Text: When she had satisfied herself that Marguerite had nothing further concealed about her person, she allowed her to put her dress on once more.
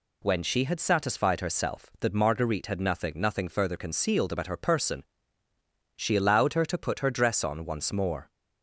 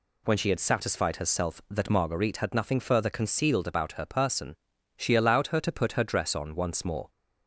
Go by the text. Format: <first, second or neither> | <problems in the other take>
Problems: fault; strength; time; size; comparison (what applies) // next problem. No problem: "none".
second | says "nothing" twice; at 3.1 s